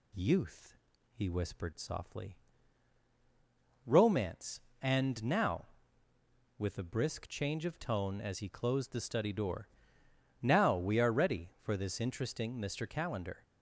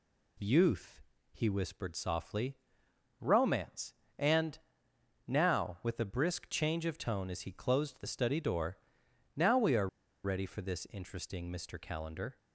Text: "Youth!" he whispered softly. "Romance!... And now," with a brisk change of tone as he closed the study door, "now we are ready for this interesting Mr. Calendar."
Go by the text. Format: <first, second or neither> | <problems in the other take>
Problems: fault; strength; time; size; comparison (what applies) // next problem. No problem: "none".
first | pauses between "And" and "now"; noticeable; at 4.5 s; 0.70 s long // pauses between "are" and "ready"; slight; at 9.8 s; 0.35 s long